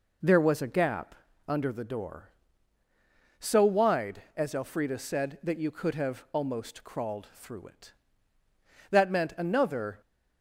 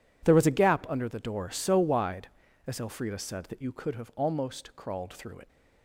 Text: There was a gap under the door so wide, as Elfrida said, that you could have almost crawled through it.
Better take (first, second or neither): second